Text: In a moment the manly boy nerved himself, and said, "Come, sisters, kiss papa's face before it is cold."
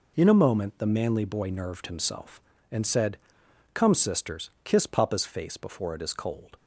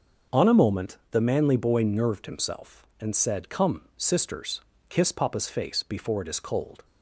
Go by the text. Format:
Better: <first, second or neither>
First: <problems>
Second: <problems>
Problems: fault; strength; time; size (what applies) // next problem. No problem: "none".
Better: first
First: none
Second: says "On" for "In"; at 0.3 s